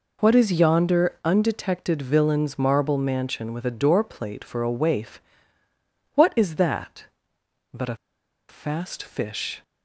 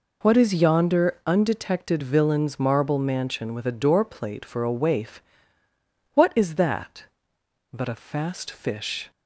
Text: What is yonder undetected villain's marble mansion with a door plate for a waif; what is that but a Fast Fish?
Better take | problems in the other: second | pauses between "a" and "Fast"; noticeable; at 7.9 s; 0.52 s long

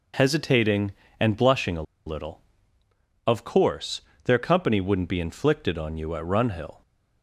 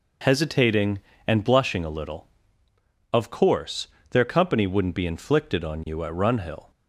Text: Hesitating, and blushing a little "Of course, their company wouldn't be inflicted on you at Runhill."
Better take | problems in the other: second | pauses between "a" and "little"; slight; at 1.8 s; 0.23 s long

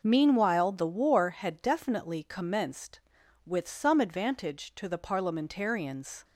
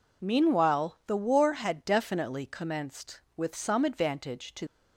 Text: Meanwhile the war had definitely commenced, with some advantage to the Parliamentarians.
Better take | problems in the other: first | stops before "the Parliamentarians"; at 4.6 s

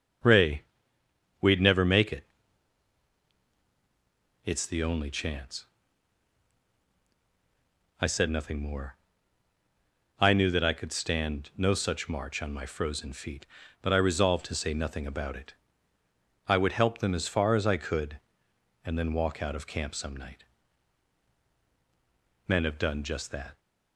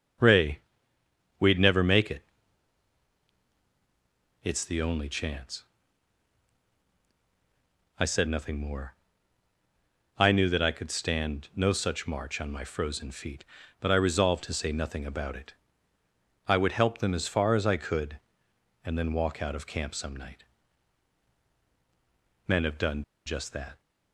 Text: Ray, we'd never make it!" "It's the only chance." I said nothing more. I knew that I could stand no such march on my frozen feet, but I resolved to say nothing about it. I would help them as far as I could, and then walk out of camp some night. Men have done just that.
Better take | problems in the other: first | starts louder than the rest; strong; until 1.9 s; 7.5 dB; strong in the first // pauses between "done" and "just"; slight; at 23.0 s; 0.22 s long

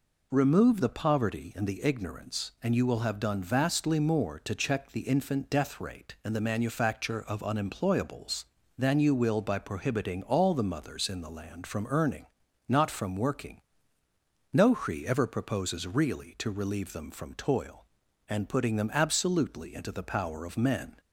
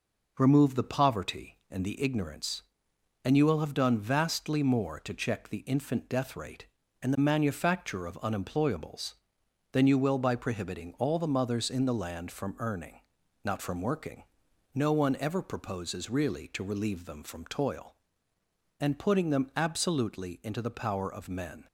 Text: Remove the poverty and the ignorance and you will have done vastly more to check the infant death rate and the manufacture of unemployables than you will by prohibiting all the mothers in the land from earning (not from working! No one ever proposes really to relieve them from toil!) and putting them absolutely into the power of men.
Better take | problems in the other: second | says "hri" for "one"; at 14.7 s

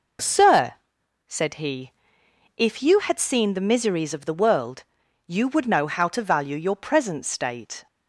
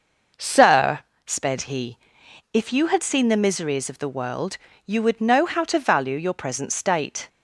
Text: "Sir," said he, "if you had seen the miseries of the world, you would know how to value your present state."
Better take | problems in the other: first | says "sped" for "said"; at 1.2 s

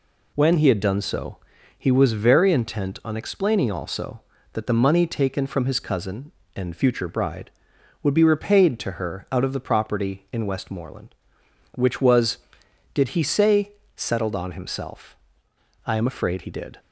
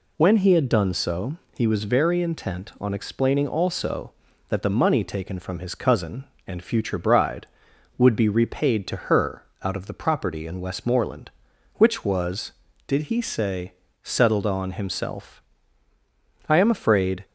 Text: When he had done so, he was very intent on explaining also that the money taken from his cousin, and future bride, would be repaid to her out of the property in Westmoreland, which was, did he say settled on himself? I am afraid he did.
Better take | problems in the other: first | pauses between "her" and "out"; slight; at 9.4 s; 0.20 s long // pauses between "say" and "settled"; slight; at 13.7 s; 0.30 s long; slight in the first // stops before "he did"; at 17.2 s

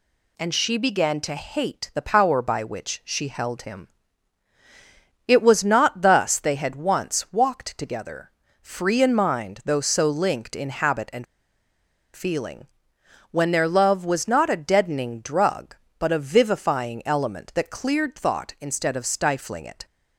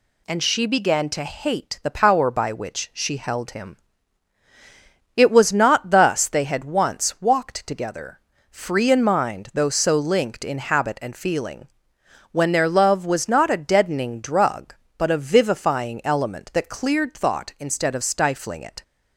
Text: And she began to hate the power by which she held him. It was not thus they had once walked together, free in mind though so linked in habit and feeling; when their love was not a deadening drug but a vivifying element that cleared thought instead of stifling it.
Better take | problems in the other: second | pauses between "and" and "feeling"; noticeable; at 11.2 s; 0.89 s long

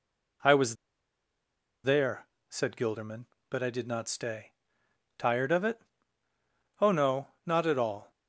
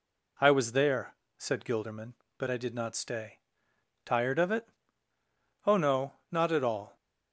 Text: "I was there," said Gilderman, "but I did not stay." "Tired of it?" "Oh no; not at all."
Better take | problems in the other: second | pauses between "was" and "there"; at 0.7 s; 1.0 s long

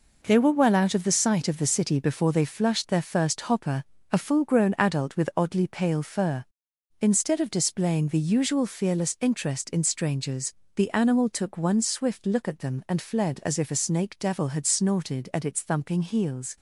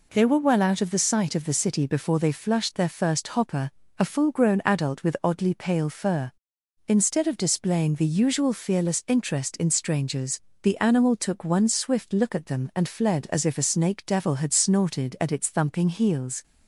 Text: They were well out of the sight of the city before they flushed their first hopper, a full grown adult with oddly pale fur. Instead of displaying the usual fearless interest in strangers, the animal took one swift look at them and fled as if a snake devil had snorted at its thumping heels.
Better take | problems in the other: second | gets quieter; throughout; 7 dB

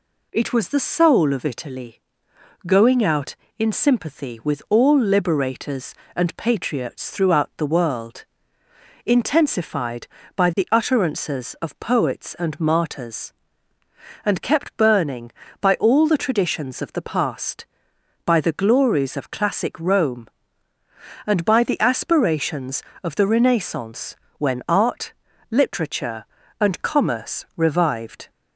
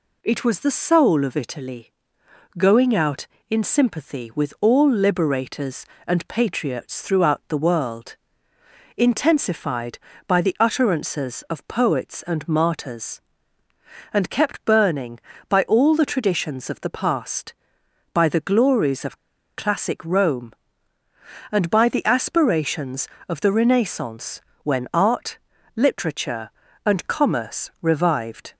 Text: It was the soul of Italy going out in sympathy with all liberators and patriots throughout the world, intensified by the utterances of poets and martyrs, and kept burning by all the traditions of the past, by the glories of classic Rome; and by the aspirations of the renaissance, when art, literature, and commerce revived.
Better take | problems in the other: first | pauses between "Italy" and "going"; noticeable; at 1.9 s; 0.66 s long; noticeable in the first // pauses between "of" and "classic"; at 19.1 s; 0.37 s long

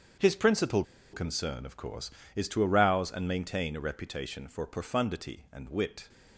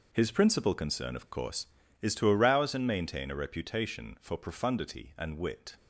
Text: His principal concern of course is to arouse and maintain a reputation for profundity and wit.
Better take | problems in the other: second | starts louder than the rest; strong; until 1.4 s; 7 dB // pauses between "principal" and "concern"; slight; at 0.8 s; 0.30 s long

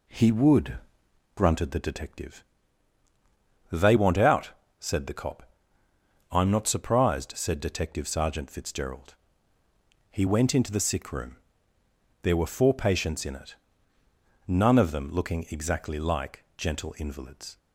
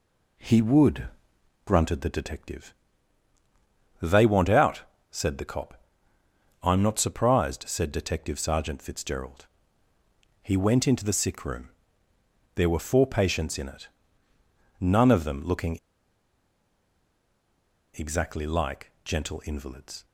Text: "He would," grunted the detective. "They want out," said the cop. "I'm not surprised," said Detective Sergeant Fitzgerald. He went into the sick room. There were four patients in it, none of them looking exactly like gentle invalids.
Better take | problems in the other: first | pauses between "looking" and "exactly"; strong; at 15.7 s; 2.1 s long

